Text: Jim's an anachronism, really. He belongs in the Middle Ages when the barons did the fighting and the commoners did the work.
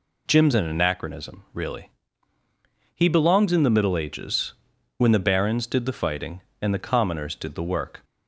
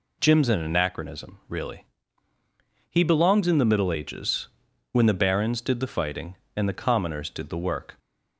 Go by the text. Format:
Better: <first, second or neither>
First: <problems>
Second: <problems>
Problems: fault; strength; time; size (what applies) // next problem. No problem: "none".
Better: neither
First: pauses between "Ages" and "when"; at 4.5 s; 0.42 s long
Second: pauses between "Ages" and "when"; at 4.4 s; 0.42 s long